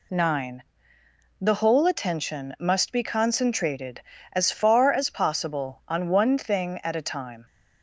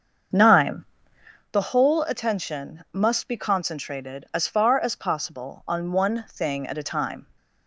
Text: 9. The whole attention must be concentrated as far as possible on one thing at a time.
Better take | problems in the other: first | starts louder than the rest; until 1.5 s; 7 dB

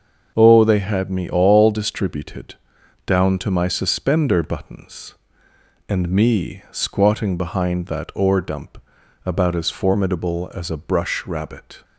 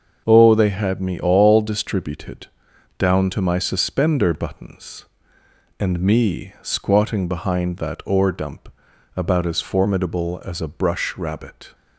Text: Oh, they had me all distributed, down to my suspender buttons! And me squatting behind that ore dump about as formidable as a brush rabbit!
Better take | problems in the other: neither | starts louder than the rest; the same in both // pauses between "dump" and "about"; noticeable; the same in both

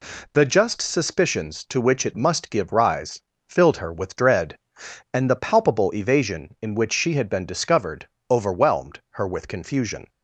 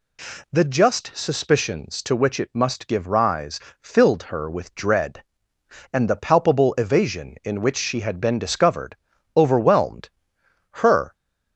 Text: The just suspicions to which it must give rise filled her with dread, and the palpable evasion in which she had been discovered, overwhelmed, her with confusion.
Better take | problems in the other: first | pauses between "rise" and "filled"; slight; at 3.5 s; 0.22 s long; slight in the first // stops before "with confusion"; at 11.1 s

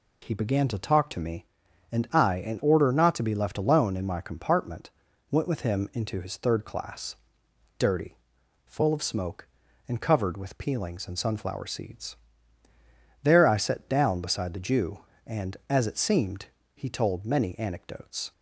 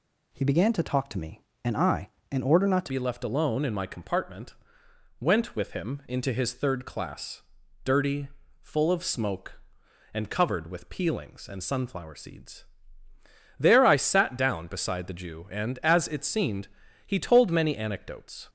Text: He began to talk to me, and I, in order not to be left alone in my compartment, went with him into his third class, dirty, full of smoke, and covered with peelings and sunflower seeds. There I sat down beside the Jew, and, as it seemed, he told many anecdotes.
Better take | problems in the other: first | changes voice at "be"; from 2.8 s on; 15.6 s long

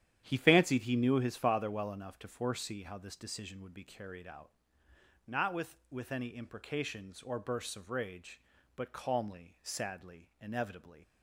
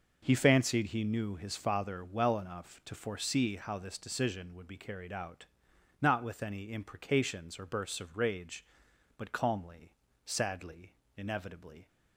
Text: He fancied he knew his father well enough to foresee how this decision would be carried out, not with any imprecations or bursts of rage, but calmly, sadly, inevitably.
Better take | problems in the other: second | starts louder than the rest; strong; until 1.2 s; 10.5 dB // says "with" twice; at 5.9 s

